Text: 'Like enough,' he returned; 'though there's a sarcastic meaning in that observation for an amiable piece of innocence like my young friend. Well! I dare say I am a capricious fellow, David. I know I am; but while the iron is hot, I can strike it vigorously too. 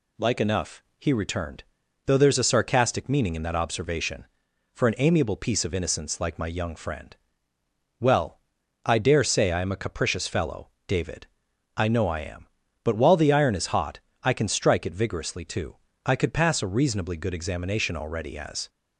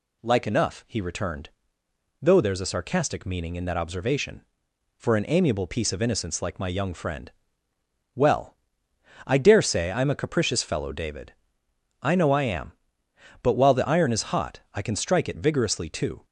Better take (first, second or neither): second